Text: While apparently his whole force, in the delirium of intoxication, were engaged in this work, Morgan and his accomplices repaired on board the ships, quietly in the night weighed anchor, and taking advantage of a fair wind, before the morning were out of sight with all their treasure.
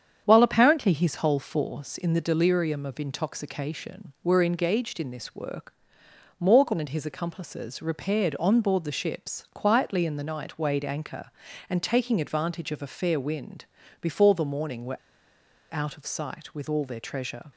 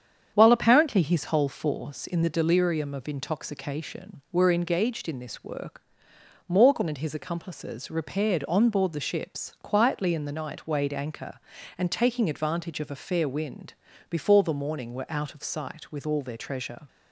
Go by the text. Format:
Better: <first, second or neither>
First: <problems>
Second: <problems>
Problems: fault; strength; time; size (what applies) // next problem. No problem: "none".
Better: second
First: starts louder than the rest; strong; until 1.2 s; 8 dB // pauses between "were" and "out"; noticeable; at 14.9 s; 0.75 s long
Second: starts louder than the rest; strong; until 1.3 s; 8 dB